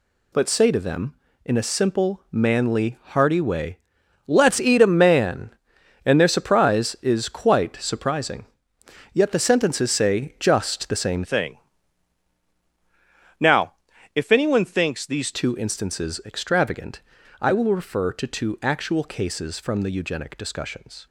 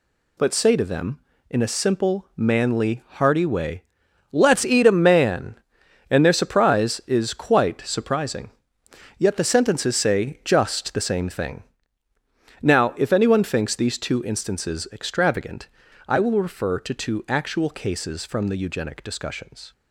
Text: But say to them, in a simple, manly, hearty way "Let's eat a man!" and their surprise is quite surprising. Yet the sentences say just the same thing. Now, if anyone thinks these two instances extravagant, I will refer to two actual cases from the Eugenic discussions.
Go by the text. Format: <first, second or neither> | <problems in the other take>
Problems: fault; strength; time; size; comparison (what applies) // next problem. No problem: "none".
second | pauses between "way" and "Let's"; noticeable; at 3.7 s; 0.48 s long; noticeable in the second // changes voice from "thing" to "these"; from 11.2 to 15.3 s; 4.1 s long